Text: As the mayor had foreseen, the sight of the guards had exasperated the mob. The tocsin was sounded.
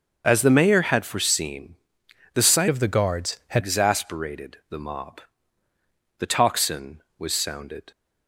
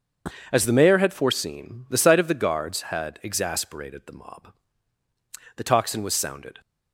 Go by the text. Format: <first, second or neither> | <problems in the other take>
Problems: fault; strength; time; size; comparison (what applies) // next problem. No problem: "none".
second | starts louder than the rest; until 1.2 s; 6.5 dB // changes voice from "of" to "had"; from 2.6 to 3.6 s; 1.0 s long